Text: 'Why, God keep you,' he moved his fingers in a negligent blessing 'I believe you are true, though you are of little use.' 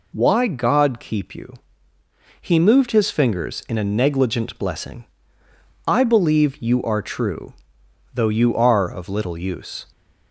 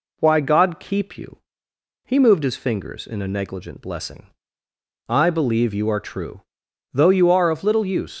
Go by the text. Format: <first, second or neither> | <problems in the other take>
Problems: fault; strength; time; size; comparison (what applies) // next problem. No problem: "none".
first | pauses between "blessing" and "I"; noticeable; at 4.2 s; 0.80 s long; noticeable in the first // leaves "use" unfinished; at 8.1 s; 110 ms